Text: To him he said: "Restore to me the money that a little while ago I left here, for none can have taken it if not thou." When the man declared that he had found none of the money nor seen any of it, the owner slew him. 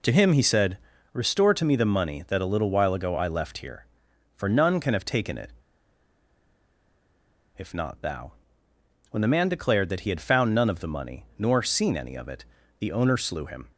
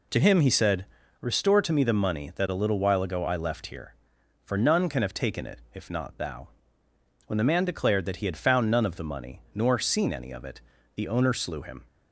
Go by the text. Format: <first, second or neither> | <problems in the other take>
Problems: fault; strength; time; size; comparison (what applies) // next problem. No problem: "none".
second | pauses between "it" and "if"; strong; at 5.5 s; 2.0 s long